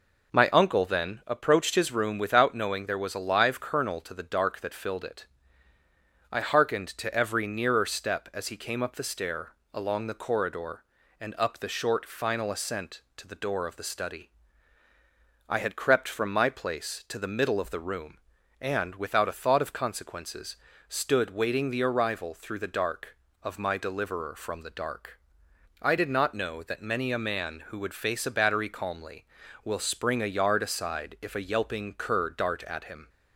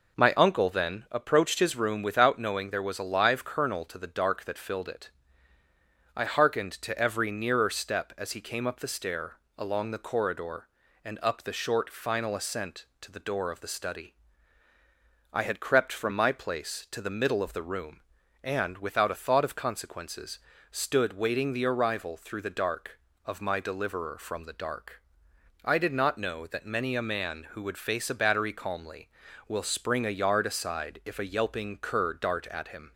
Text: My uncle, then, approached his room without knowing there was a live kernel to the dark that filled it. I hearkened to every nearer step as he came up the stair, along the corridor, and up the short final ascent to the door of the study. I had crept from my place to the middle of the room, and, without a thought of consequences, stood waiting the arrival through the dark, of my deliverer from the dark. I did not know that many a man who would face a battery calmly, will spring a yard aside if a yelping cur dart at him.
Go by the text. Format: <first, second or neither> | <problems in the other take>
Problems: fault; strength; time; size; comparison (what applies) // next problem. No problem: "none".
neither | none